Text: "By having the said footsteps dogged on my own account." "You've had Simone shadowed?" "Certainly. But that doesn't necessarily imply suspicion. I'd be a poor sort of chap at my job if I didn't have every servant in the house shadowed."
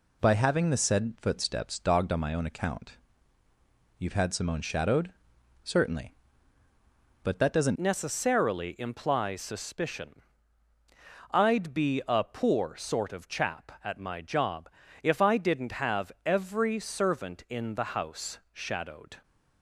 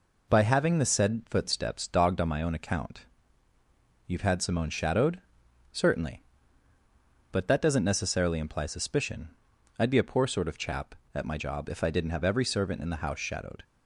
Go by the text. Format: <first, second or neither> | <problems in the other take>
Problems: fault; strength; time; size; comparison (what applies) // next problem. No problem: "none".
second | changes voice at "necessarily"; from 7.7 s on; 11.5 s long // pauses between "job" and "if"; slight; at 14.6 s; 0.34 s long